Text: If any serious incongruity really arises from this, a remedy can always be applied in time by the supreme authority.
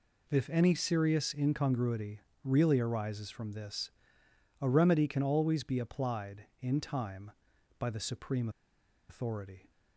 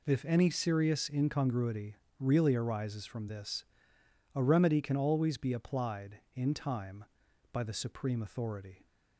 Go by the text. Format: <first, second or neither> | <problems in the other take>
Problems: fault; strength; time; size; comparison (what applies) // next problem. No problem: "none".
second | pauses between "incongruity" and "really"; slight; at 2.1 s; 0.24 s long; slight in the second // pauses between "supreme" and "authority"; noticeable; at 8.4 s; 0.60 s long